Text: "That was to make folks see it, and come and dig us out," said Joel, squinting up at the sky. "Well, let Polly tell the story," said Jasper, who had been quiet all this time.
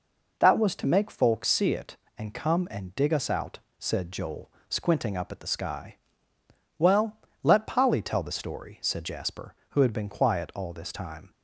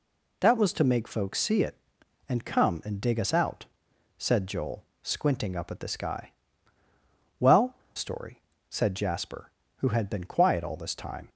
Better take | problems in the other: first | skips "let Polly tell the"; at 7.8 s

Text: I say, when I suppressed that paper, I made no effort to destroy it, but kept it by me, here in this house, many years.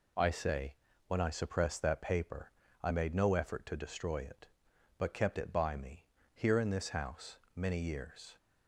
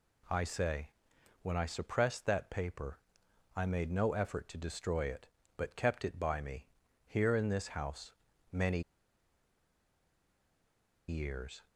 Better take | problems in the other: first | pauses between "many" and "years"; strong; at 8.8 s; 2.2 s long

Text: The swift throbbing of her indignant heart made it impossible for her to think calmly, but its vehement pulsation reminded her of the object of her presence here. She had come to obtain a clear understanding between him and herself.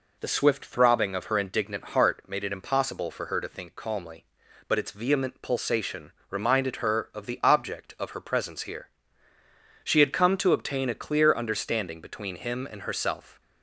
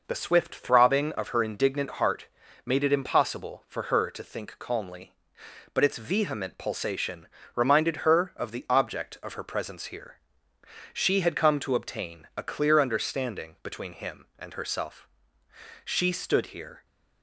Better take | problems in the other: first | pauses between "heart" and "made"; at 2.2 s; 0.38 s long // pauses between "pulsation" and "reminded"; slight; at 7.2 s; 0.28 s long; slight in the first // goes on to say "She stood here"; noticeable; from 15.8 s on; 1.0 s long

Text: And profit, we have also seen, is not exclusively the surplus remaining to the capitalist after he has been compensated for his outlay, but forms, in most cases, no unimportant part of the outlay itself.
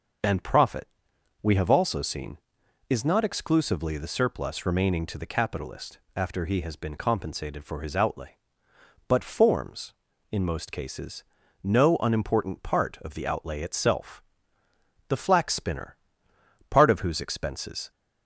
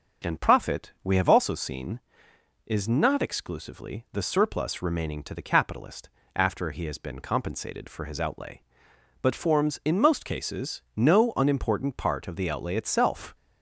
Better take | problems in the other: second | starts louder than the rest; noticeable; until 1.7 s; 6 dB // pauses between "capitalist" and "after"; slight; at 5.9 s; 0.16 s long; slight in the second // goes on to say "The flax spinner part of whose expenses"; strong; from 15.0 s on; 2.8 s long

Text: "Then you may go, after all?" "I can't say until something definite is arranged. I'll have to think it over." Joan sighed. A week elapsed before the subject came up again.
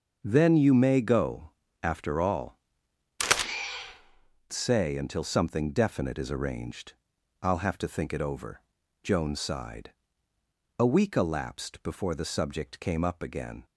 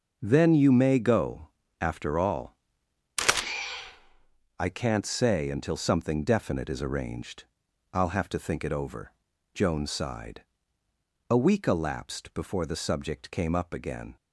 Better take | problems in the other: second | starts louder than the rest; until 1.2 s; 7 dB; also in the second // skips "I can't"; at 3.5 s

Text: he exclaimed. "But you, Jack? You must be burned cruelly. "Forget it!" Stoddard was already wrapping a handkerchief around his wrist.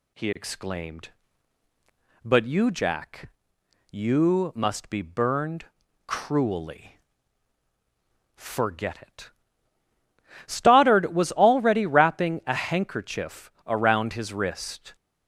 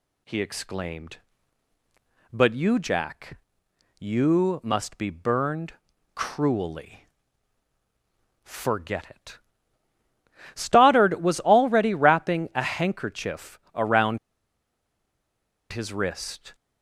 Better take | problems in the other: first | pauses between "burned" and "cruelly"; at 5.7 s; 0.42 s long; also in the first // pauses between "handkerchief" and "around"; slight; at 13.5 s; 0.16 s long; slight in the first // pauses between "around" and "his"; strong; at 14.1 s; 1.5 s long

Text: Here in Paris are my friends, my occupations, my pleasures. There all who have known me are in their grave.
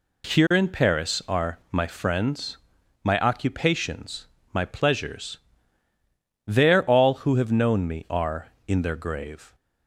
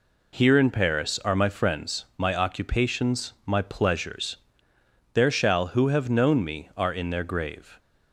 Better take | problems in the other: first | says "shall" for "all"; at 5.3 s

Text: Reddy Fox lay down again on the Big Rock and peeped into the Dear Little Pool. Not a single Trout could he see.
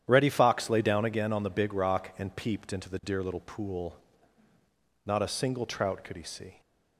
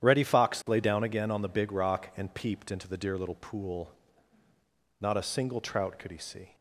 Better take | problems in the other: neither | starts louder than the rest; strong; the same in both

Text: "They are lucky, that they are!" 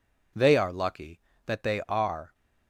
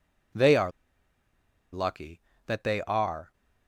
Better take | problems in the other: first | pauses between "are" and "lucky"; at 0.7 s; 1.0 s long

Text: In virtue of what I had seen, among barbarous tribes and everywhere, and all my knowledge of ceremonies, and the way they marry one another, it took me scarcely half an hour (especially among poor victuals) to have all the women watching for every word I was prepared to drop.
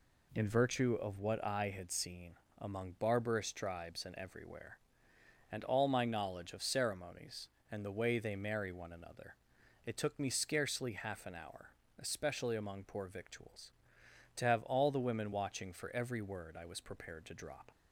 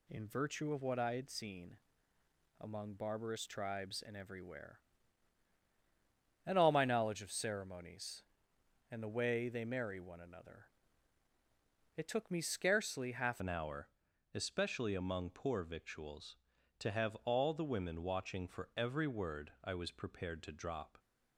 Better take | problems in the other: first | changes voice at "an"; from 13.4 s on; 7.5 s long

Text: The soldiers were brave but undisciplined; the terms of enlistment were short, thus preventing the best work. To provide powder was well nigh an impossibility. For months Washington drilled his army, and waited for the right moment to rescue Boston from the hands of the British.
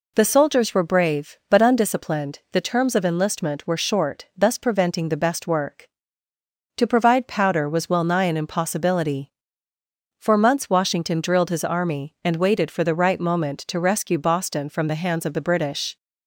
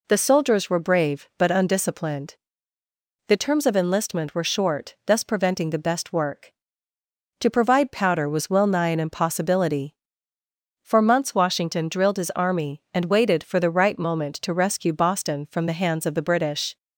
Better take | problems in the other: neither | none

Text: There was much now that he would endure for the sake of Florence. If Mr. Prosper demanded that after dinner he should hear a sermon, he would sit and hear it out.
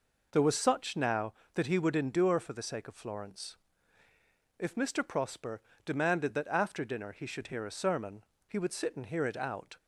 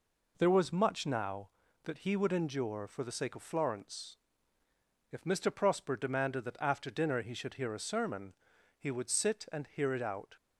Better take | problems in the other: second | says "such" for "much"; at 0.5 s // pauses between "Prosper" and "demanded"; slight; at 5.6 s; 0.24 s long

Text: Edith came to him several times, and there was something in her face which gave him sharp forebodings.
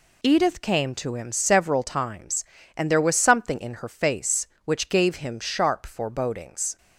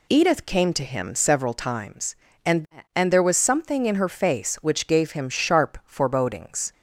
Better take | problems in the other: first | says "and" twice; at 2.9 s

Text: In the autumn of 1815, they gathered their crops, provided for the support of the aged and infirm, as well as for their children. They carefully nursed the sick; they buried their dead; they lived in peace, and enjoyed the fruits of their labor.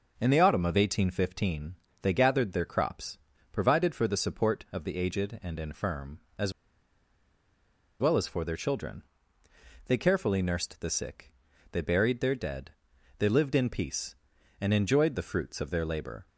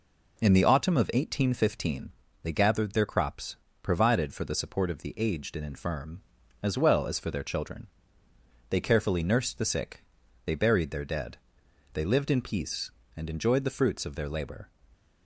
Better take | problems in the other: second | starts louder than the rest; noticeable; until 1.1 s; 6 dB // pauses between "as" and "well"; strong; at 6.5 s; 1.4 s long

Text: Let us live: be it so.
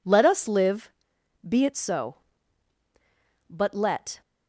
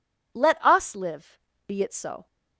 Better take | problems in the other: second | goes on to say "But let"; noticeable; from 3.5 s on; 0.70 s long

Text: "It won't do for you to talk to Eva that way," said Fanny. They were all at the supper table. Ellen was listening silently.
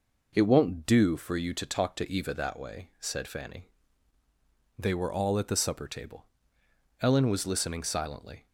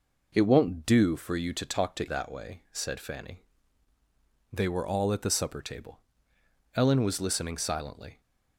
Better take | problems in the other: first | skips "Eva"; at 2.0 s

